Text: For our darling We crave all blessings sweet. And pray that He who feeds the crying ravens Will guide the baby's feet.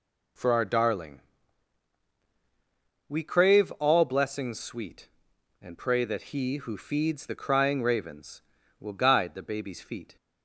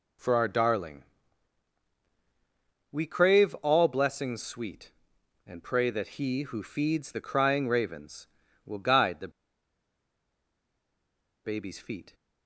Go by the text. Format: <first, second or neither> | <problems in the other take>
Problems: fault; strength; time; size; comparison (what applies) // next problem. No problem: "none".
first | pauses between "darling" and "We"; strong; at 1.0 s; 1.8 s long; strong in the first // pauses between "the" and "baby's"; strong; at 9.2 s; 2.1 s long